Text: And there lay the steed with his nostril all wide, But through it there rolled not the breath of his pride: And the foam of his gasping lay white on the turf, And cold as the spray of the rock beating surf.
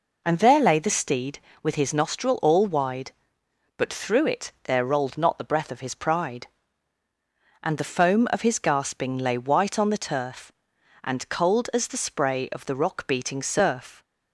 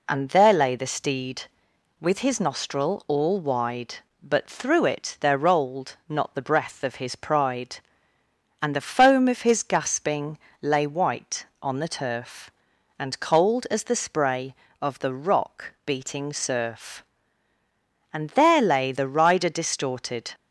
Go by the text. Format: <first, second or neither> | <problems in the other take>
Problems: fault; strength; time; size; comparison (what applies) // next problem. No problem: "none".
first | pauses between "gasping" and "lay"; slight; at 10.3 s; 0.24 s long // goes on to say "And there lay the rider distorted"; strong; from 18.1 s on; 2.2 s long